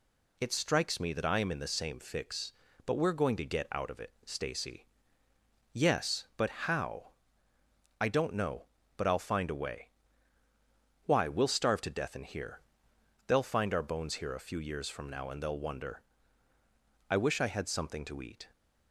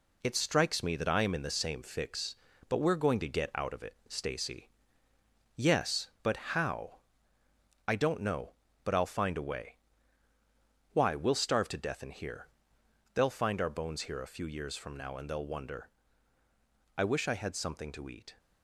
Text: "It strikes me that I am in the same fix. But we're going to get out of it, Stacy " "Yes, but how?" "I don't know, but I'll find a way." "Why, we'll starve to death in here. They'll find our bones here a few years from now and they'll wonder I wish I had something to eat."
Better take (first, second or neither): first